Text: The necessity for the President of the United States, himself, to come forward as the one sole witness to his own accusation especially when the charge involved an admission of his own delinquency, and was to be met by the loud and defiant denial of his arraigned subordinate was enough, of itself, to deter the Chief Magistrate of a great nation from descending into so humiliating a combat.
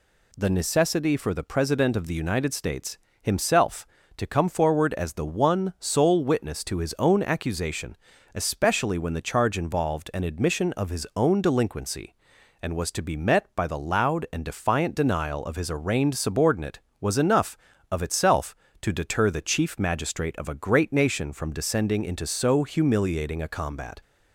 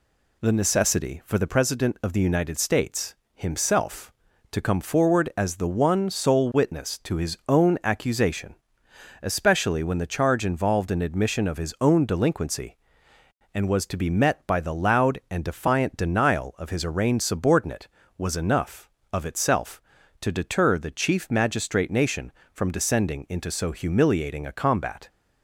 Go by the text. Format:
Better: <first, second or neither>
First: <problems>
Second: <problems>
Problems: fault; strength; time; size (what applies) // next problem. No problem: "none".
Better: first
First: pauses between "accusation" and "especially"; slight; at 7.9 s; 0.36 s long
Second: pauses between "accusation" and "especially"; noticeable; at 8.5 s; 0.68 s long // skips "of a great"; at 21.9 s